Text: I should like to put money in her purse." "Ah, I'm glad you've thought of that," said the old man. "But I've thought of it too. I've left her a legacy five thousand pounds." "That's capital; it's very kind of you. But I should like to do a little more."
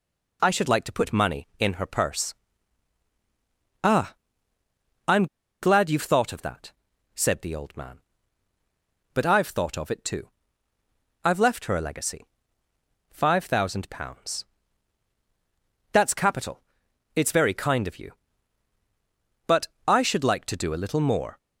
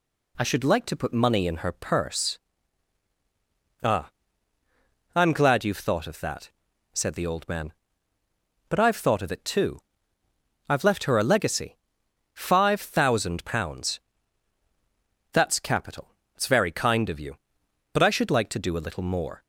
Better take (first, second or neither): second